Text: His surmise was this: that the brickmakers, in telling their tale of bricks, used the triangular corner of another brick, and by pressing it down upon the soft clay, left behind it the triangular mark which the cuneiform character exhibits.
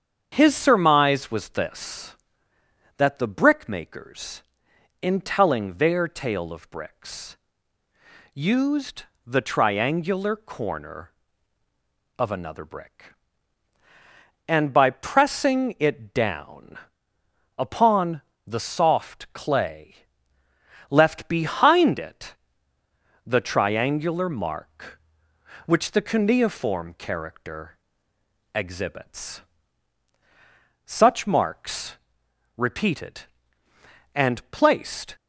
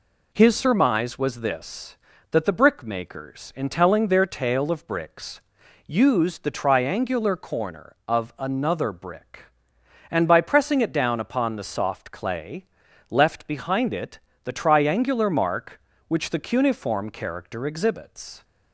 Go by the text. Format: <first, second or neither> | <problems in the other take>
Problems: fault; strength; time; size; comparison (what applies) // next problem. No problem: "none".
second | starts louder than the rest; strong; until 1.3 s; 7.5 dB // pauses between "used" and "the"; slight; at 9.0 s; 0.24 s long // pauses between "down" and "upon"; noticeable; at 16.7 s; 0.80 s long // pauses between "upon" and "the"; slight; at 18.2 s; 0.26 s long // pauses between "it" and "the"; noticeable; at 22.3 s; 0.90 s long; slight in the second // pauses between "character" and "exhibits"; noticeable; at 27.7 s; 0.78 s long // goes on to say "Such marks repeated and placed"; strong; from 30.8 s on; 4.3 s long